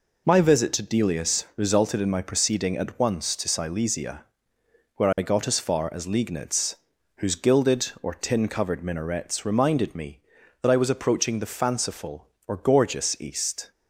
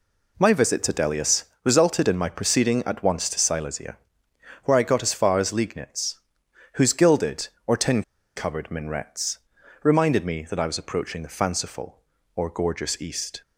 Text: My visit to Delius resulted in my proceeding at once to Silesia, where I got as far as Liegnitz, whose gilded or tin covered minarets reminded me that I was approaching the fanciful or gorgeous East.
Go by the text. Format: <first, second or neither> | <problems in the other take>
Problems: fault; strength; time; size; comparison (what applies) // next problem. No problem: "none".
first | pauses between "Delius" and "resulted"; slight; at 1.4 s; 0.20 s long // pauses between "tin" and "covered"; slight; at 8.0 s; 0.34 s long // pauses between "minarets" and "reminded"; at 9.3 s; 0.44 s long